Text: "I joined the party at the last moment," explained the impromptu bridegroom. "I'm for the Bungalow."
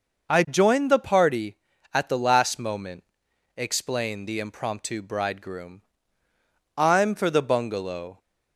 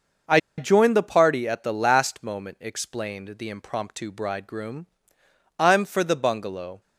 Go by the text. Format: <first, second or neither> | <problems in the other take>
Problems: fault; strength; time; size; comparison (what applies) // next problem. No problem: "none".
first | pauses between "I" and "joined"; slight; at 0.3 s; 0.19 s long